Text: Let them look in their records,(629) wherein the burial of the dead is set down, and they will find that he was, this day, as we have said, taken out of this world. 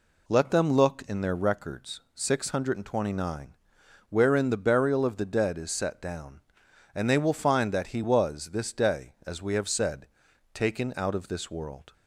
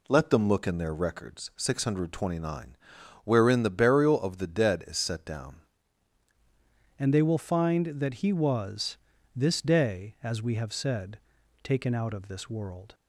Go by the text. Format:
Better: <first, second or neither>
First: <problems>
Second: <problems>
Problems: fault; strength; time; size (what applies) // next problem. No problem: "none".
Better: first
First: none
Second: changes voice at "and"; from 6.9 s on; 6.0 s long